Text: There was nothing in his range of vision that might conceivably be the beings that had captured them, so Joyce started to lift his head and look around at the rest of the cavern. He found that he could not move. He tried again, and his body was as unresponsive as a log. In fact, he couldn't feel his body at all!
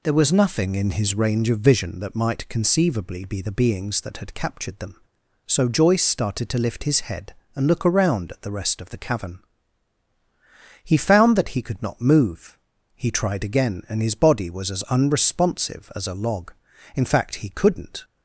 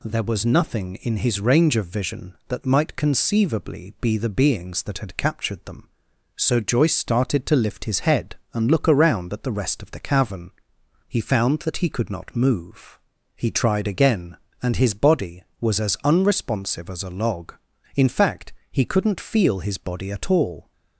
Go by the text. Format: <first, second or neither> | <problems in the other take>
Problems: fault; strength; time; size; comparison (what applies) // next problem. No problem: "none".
second | stops before "feel his body at all"; at 18.0 s